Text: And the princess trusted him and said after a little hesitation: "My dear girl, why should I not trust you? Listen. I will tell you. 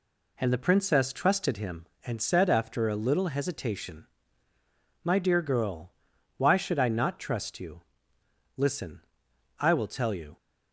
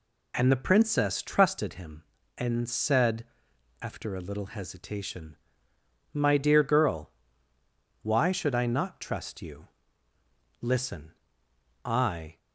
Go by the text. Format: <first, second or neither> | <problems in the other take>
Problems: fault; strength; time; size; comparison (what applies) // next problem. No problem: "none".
first | pauses between "said" and "after"; noticeable; at 3.2 s; 0.58 s long // stops before "will tell you"; at 12.3 s